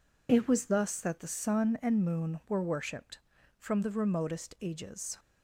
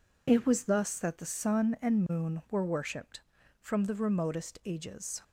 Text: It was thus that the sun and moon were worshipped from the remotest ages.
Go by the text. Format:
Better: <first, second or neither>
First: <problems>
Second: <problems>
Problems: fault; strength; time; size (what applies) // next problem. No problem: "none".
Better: neither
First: none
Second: none